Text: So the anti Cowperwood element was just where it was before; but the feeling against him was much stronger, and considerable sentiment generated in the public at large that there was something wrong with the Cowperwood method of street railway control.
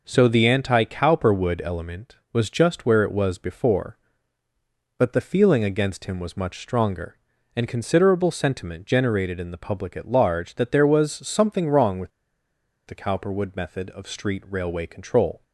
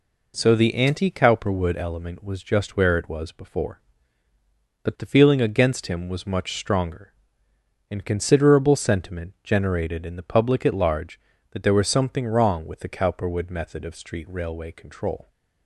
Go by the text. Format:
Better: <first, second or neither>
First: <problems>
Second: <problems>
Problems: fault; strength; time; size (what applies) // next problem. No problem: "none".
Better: second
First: pauses between "with" and "the"; noticeable; at 12.1 s; 0.76 s long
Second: none